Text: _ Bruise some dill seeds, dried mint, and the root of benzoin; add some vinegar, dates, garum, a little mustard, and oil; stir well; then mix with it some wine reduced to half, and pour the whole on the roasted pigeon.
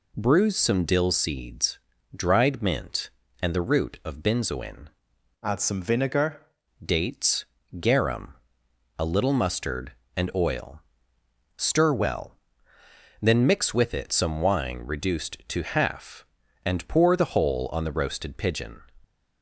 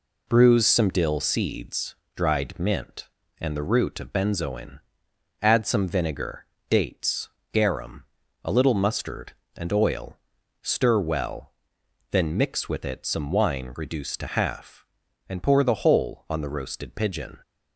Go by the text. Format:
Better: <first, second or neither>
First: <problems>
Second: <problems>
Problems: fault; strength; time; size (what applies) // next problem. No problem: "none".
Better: second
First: changes voice from "add" to "vinegar"; from 5.4 to 6.4 s; 1.0 s long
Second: none